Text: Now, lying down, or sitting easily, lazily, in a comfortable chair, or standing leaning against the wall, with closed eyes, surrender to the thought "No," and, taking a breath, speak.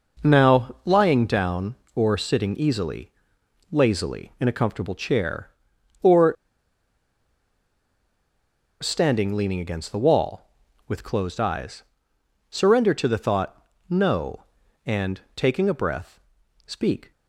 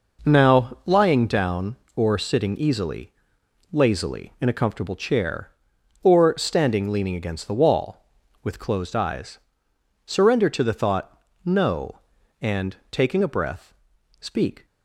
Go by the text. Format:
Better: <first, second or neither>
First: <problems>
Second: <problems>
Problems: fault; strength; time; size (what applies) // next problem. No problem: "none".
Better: second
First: pauses between "or" and "standing"; strong; at 6.3 s; 2.4 s long // pauses between "thought" and "No"; slight; at 13.6 s; 0.24 s long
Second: pauses between "thought" and "No"; slight; at 11.2 s; 0.24 s long